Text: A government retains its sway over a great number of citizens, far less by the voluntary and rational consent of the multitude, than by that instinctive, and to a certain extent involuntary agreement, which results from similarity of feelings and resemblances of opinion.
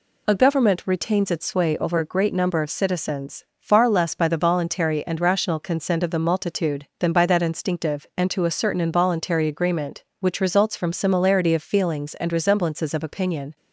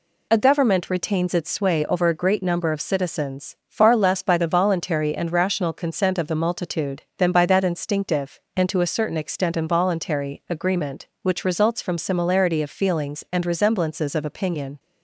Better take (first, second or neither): second